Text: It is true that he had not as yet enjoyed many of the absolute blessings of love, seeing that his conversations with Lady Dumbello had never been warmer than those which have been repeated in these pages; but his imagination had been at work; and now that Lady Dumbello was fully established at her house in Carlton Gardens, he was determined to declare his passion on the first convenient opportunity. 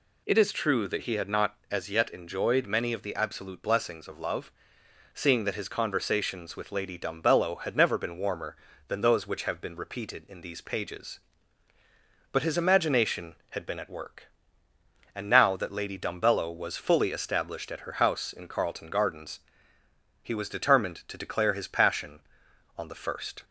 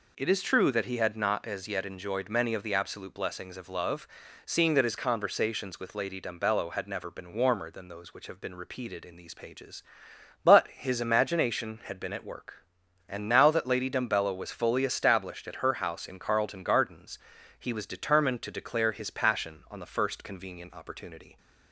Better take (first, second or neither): second